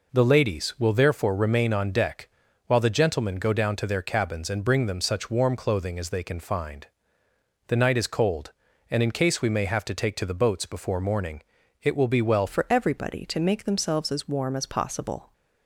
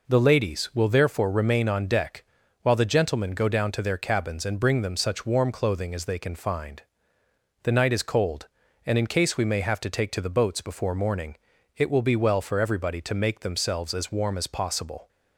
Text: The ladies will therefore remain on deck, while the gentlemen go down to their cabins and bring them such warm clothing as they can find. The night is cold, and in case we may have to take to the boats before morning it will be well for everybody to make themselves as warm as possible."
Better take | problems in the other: second | pauses between "morning" and "it"; at 11.4 s; 0.40 s long; also in the second // changes voice at "for"; from 12.4 s on; 2.9 s long

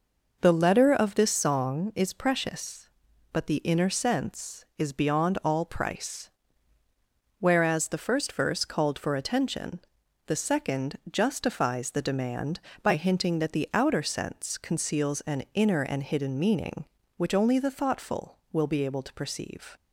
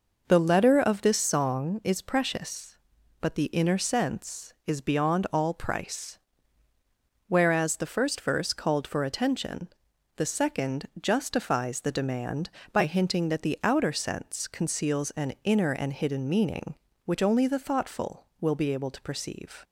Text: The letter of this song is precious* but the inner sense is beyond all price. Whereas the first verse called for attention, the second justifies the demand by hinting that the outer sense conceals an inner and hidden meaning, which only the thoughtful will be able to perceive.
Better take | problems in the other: neither | none

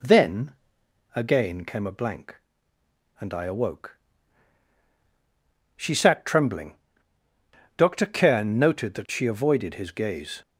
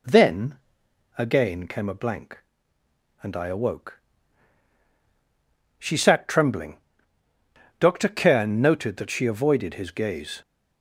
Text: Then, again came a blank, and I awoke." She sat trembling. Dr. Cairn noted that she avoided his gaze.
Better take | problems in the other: neither | none

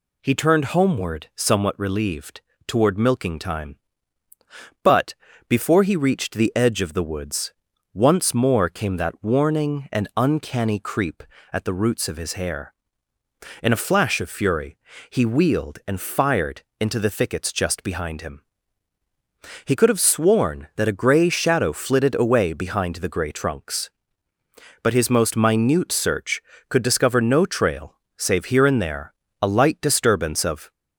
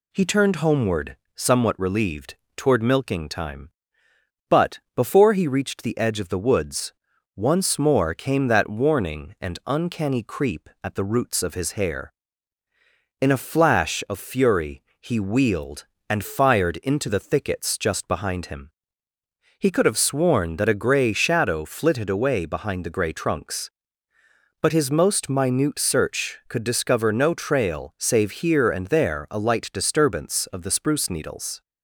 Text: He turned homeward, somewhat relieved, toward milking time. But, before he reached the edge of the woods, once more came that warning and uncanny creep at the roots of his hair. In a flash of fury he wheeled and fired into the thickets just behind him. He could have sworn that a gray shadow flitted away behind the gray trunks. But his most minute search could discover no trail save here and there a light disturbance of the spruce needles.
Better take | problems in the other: second | pauses between "fury" and "he"; slight; at 14.7 s; 0.32 s long; slight in the second // pauses between "fired" and "into"; slight; at 16.6 s; 0.18 s long // pauses between "trail" and "save"; slight; at 27.9 s; 0.22 s long // pauses between "there" and "a"; slight; at 29.1 s; 0.28 s long // stops before "the spruce needles"; at 30.7 s

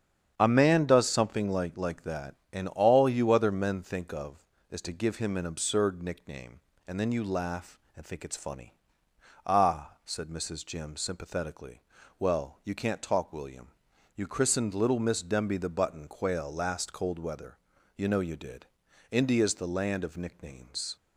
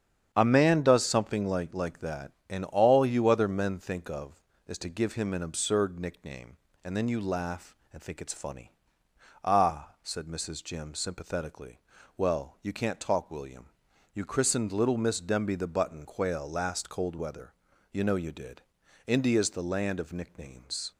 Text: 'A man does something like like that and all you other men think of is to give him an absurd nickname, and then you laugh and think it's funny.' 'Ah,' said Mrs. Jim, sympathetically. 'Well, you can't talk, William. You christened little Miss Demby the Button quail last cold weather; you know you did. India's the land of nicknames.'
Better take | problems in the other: neither | starts louder than the rest; strong; the same in both

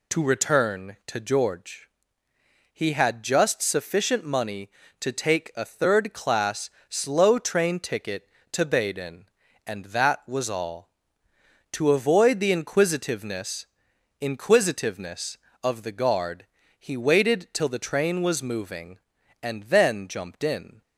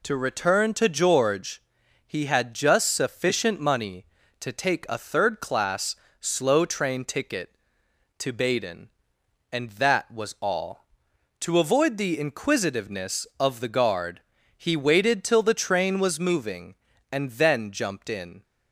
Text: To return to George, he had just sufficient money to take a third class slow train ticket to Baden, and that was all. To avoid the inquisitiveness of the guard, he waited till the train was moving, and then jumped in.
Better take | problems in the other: second | pauses between "class" and "slow"; slight; at 6.6 s; 0.20 s long; slight in the second // says "inquisitiveness" twice; at 14.1 s

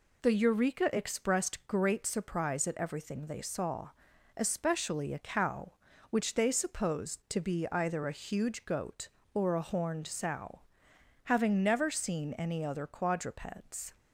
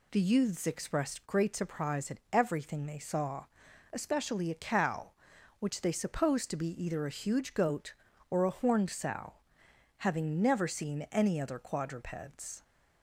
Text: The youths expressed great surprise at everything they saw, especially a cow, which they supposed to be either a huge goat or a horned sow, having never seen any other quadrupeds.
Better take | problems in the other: second | says "eureka" for "youths"; at 0.3 s

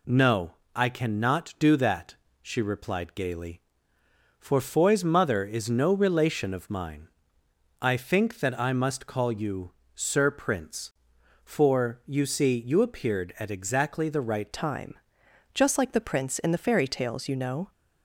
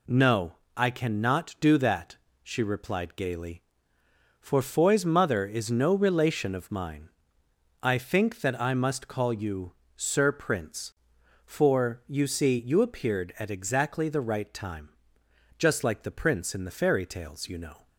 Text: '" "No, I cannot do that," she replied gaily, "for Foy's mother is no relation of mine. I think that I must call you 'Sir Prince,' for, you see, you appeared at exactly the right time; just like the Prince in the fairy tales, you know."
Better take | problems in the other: second | pauses between "you" and "Sir"; slight; at 9.7 s; 0.24 s long; slight in the second // changes voice at "time"; from 14.5 s on; 3.2 s long

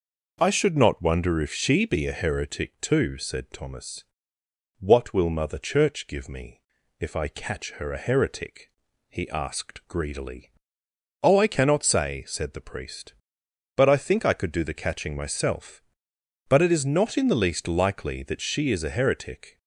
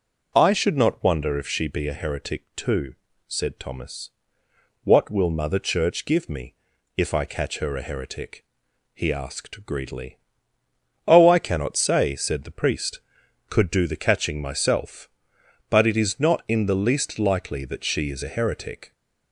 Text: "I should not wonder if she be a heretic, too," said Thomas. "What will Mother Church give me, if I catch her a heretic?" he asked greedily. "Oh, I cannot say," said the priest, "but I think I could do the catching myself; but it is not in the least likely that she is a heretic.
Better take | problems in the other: first | skips "but I think I"; at 13.2 s

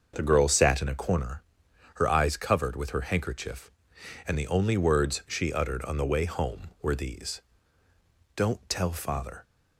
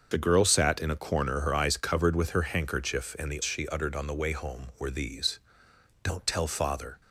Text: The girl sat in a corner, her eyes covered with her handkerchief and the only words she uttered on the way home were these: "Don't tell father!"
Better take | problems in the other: first | starts louder than the rest; until 1.1 s; 6.5 dB; also in the first // skips "only words"; at 3.4 s

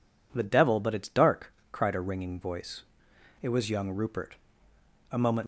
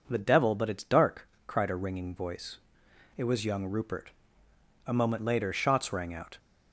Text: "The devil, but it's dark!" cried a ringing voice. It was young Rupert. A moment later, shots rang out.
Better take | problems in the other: second | stops before "later shots rang out"; at 5.4 s

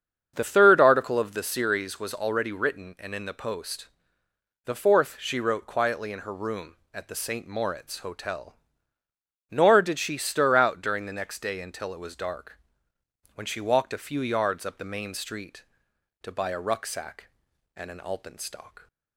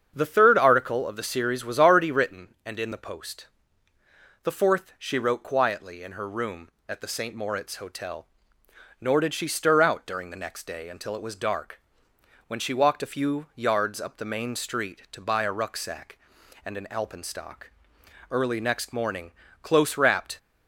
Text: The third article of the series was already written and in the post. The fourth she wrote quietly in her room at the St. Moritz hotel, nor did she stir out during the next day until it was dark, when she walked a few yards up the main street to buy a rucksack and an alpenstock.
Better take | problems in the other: first | starts louder than the rest; strong; until 1.1 s; 7.5 dB; strong in the first // goes on to say "Early next morning close wrapped"; strong; from 18.2 s on; 2.0 s long

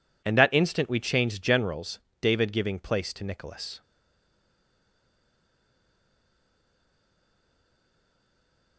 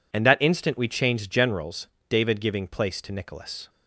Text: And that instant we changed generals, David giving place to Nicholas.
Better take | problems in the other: second | stays silent after the last word; strong; from 3.8 s on; 4.9 s long

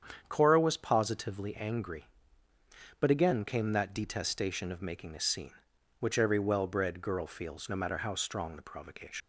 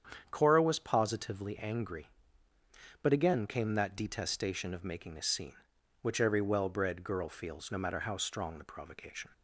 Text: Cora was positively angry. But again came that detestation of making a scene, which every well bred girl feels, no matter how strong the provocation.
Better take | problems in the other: second | starts louder than the rest; strong; until 1.2 s; 8 dB; strong in the second // leaves "provocation" unfinished; at 9.2 s; 100 ms

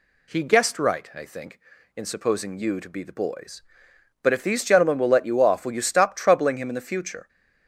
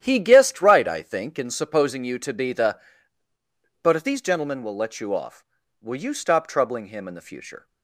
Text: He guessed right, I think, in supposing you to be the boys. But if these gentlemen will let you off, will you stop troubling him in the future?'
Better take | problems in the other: first | starts louder than the rest; strong; until 1.0 s; 10.5 dB // skips "boys"; at 3.3 s

